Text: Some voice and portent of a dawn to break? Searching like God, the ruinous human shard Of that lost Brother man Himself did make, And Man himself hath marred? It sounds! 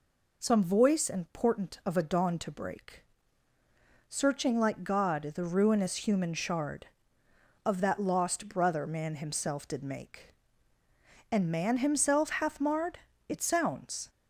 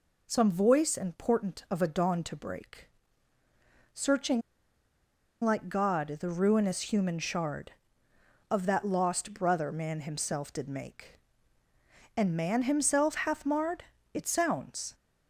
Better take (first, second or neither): first